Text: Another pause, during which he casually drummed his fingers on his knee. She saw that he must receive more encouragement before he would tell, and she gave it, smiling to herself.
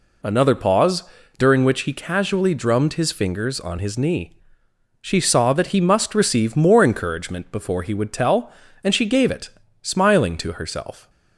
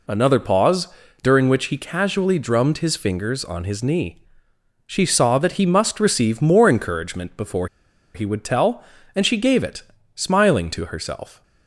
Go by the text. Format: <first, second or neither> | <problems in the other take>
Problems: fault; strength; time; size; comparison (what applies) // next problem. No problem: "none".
first | pauses between "before" and "he"; noticeable; at 7.6 s; 0.48 s long